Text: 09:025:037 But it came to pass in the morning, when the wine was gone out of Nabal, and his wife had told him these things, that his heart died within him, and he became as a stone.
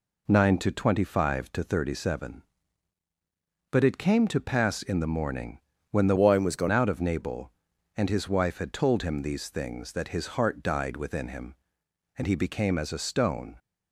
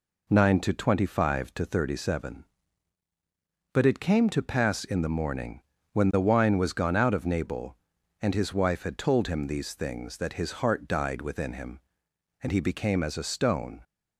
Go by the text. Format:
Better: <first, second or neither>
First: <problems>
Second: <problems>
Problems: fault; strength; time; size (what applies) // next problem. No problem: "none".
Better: second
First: changes voice from "wine" to "gone"; from 6.1 to 6.6 s; 0.5 s long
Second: none